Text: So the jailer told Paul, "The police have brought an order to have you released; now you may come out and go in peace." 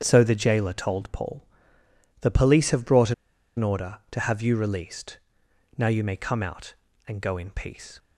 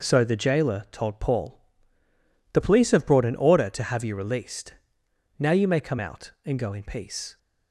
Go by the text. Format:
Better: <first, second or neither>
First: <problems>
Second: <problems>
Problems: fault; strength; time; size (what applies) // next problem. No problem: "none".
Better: second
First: starts louder than the rest; strong; until 1.0 s; 8.5 dB // pauses between "brought" and "an"; at 3.1 s; 0.44 s long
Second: none